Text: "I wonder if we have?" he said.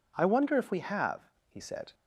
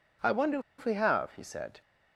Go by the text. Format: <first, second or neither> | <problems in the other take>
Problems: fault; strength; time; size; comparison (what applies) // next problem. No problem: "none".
first | pauses between "wonder" and "if"; slight; at 0.5 s; 0.18 s long